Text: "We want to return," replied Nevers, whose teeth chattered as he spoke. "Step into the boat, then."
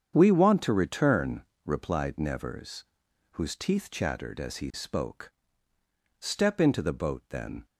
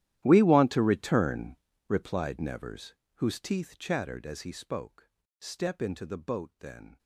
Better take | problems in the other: first | gets quieter; strong; throughout; 20 dB // starts louder than the rest; strong; until 1.2 s; 12.5 dB; strong in the first

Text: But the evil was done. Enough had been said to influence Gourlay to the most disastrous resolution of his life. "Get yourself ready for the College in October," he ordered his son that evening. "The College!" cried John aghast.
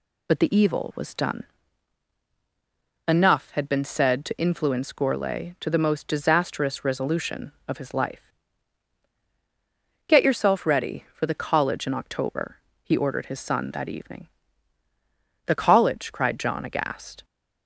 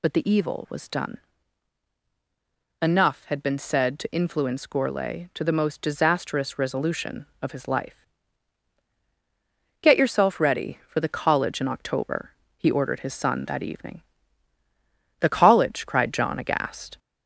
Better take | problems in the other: first | gets louder; slight; throughout; 2.5 dB

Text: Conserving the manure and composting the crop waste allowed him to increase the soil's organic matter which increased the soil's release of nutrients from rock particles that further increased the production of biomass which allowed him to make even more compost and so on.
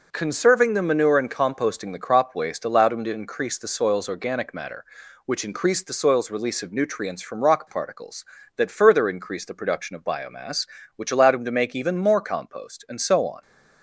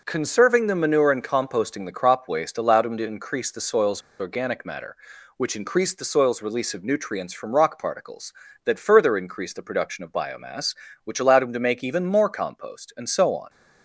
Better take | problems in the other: first | pauses between "soil's" and "organic"; slight; at 4.0 s; 0.18 s long

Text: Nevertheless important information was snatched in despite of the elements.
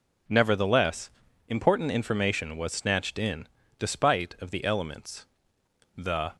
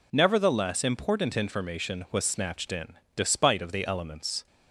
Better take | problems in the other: second | pauses between "Nevertheless" and "important"; at 1.0 s; 0.38 s long // pauses between "in" and "despite"; slight; at 3.4 s; 0.32 s long; slight in the second // goes on to say "The"; slight; from 5.9 s on; 0.40 s long

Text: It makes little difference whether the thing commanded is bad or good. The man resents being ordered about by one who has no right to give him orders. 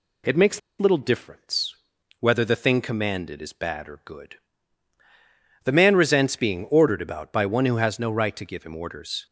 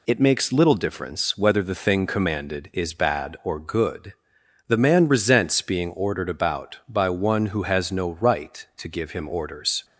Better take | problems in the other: second | pauses between "makes" and "little"; slight; at 0.5 s; 0.19 s long // pauses between "difference" and "whether"; noticeable; at 1.7 s; 0.46 s long

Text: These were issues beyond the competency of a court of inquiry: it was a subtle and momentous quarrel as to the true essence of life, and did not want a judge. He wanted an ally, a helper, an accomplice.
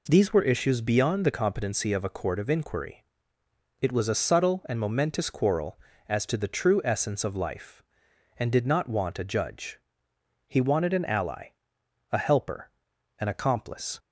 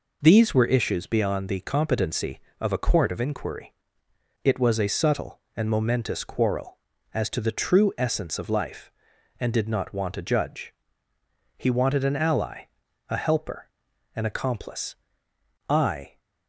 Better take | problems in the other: first | goes on to say "I"; slight; from 15.7 s on; 0.48 s long

